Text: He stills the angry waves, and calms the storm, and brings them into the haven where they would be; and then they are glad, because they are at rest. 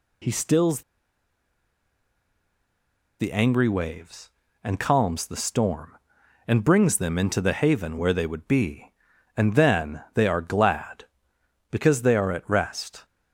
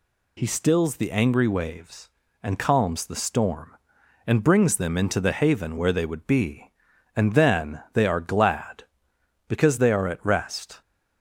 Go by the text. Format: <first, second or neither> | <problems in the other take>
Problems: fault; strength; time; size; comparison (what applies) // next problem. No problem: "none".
second | pauses between "stills" and "the"; strong; at 0.8 s; 2.3 s long